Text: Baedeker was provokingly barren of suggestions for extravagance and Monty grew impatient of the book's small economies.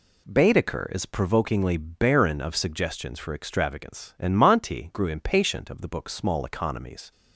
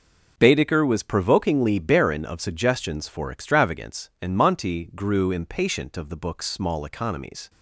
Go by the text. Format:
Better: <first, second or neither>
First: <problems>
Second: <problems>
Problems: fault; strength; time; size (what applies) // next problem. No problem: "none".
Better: second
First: says "is" for "was"; at 0.9 s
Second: none